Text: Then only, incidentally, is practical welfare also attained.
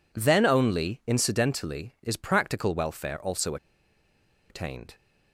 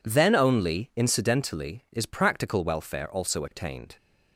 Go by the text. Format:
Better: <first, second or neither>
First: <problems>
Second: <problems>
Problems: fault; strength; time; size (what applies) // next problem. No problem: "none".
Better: second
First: pauses between "also" and "attained"; noticeable; at 3.5 s; 0.94 s long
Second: none